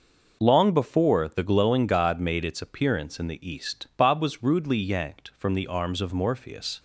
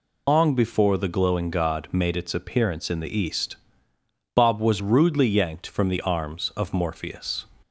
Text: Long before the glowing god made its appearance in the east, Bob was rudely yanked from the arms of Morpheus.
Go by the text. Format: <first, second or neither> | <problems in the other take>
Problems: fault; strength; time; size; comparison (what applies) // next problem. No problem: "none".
first | loses the start of "Long"; at 0.2 s; 115 ms